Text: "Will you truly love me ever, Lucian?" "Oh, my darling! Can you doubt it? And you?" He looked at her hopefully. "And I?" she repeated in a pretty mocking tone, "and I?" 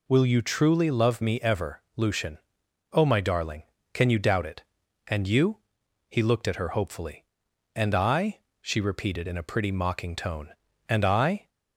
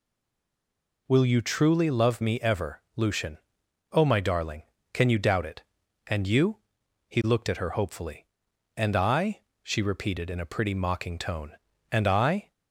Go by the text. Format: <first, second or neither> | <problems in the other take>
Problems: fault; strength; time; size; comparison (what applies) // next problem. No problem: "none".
first | stays silent before the first word; until 1.0 s; 1.0 s long